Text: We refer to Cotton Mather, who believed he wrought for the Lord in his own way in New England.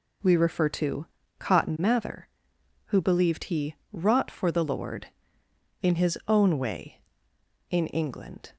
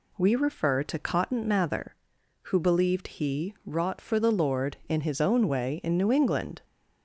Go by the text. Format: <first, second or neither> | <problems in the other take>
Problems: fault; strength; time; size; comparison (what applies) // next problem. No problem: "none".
second | pauses between "to" and "Cotton"; slight; at 1.0 s; 0.32 s long // pauses between "he" and "wrought"; slight; at 3.7 s; 0.16 s long // skips "New"; at 7.8 s